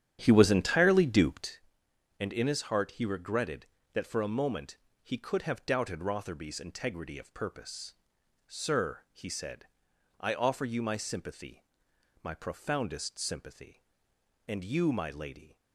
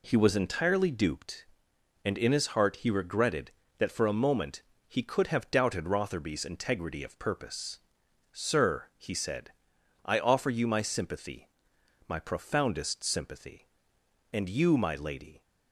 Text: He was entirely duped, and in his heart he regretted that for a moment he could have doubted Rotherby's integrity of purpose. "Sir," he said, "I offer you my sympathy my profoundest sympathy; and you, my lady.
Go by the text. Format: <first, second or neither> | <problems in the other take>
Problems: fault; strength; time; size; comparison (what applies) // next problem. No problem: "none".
second | starts louder than the rest; strong; until 1.6 s; 9.5 dB // pauses between "moment" and "he"; slight; at 4.7 s; 0.26 s long; slight in the second // pauses between "sympathy" and "my"; noticeable; at 11.6 s; 0.58 s long; noticeable in the second